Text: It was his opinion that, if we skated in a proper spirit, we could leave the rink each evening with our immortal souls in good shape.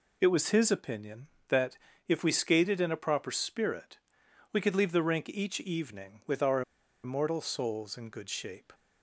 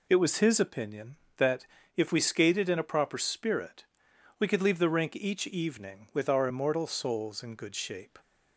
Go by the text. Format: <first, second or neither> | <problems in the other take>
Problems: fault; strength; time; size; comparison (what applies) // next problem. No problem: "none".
second | pauses between "our" and "immortal"; at 6.6 s; 0.42 s long